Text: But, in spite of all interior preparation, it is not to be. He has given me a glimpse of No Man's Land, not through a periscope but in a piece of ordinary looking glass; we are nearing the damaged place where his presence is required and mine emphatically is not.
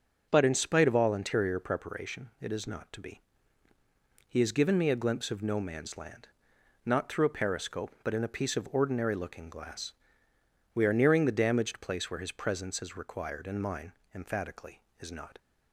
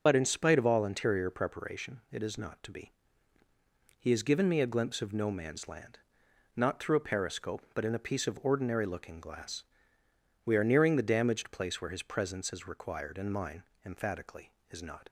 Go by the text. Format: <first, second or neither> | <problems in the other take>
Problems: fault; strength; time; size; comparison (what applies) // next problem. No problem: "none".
first | loses the start of "But"; at 0.0 s; 45 ms // starts louder than the rest; until 1.0 s; 6.5 dB; also in the first // pauses between "mine" and "emphatically"; slight; at 13.6 s; 0.22 s long; slight in the first